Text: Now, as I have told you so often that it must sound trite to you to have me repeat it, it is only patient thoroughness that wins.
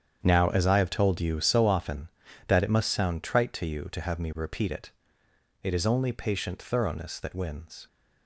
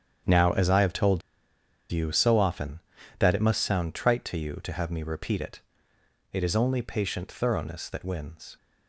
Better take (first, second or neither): first